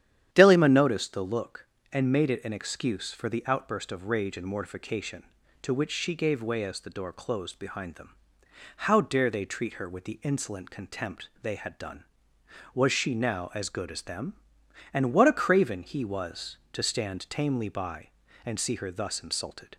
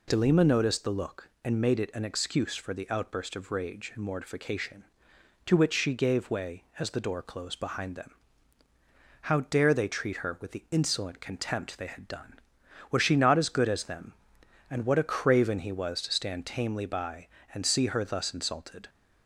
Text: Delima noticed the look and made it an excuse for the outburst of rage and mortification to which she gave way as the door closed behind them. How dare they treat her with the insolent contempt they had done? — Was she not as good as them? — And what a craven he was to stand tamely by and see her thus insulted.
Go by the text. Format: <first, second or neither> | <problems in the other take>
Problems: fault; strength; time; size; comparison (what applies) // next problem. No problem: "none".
second | starts louder than the rest; strong; until 1.3 s; 10 dB // says "now" for "not"; at 13.1 s